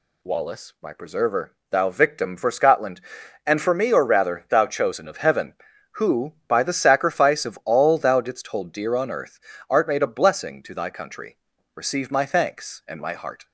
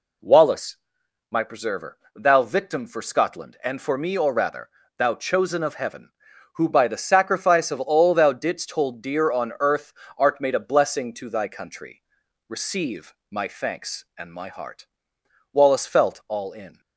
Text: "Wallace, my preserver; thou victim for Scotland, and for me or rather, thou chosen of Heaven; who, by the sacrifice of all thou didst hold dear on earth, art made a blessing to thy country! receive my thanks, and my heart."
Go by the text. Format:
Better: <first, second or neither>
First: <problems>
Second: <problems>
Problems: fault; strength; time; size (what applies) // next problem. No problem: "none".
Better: first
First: none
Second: pauses between "receive" and "my"; slight; at 13.1 s; 0.16 s long // goes on to say "Wallace felt all in"; noticeable; from 15.5 s on; 1.2 s long